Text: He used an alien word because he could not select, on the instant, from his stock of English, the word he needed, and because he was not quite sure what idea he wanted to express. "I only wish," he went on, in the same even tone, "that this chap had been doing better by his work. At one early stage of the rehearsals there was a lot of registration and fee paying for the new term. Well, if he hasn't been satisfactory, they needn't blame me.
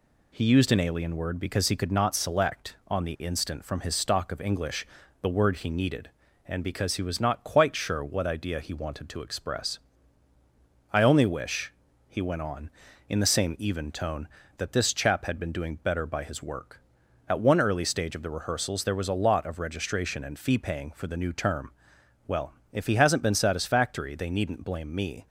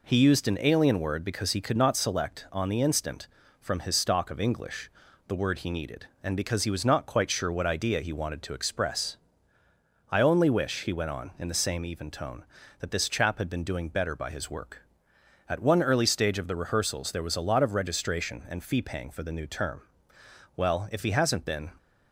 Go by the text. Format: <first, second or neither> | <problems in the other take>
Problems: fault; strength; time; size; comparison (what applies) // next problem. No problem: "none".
first | stops before "satisfactory they needn't blame me"; at 21.7 s